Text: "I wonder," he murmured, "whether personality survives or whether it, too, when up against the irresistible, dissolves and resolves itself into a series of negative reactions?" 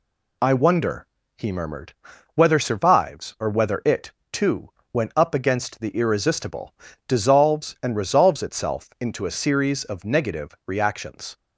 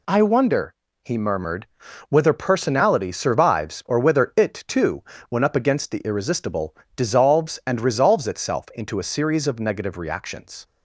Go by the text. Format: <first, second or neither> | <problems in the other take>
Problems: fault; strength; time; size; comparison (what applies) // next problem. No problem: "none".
second | skips "personality"; at 2.5 s